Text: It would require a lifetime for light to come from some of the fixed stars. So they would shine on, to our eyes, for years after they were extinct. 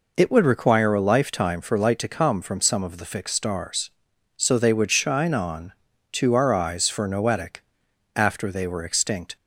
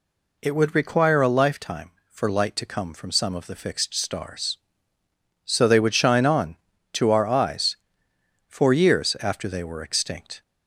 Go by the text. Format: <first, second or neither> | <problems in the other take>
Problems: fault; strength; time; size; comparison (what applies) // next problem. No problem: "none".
second | says "noetic" for "years"; at 7.0 s